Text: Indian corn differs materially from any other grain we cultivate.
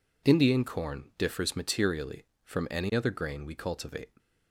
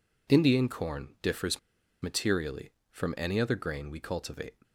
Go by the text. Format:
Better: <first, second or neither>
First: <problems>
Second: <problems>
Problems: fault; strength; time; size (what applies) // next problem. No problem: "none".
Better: first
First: none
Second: pauses between "differs" and "materially"; at 1.5 s; 0.43 s long